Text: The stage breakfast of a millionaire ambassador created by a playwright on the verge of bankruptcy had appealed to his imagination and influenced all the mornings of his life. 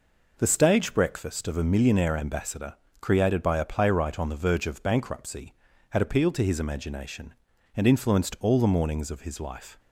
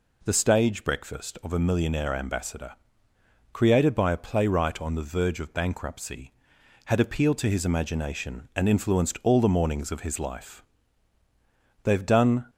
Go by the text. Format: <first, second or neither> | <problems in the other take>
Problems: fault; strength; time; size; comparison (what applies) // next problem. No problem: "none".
first | pauses between "ambassador" and "created"; noticeable; at 2.7 s; 0.78 s long; slight in the first // goes on to say "They've done"; noticeable; from 11.8 s on; 0.62 s long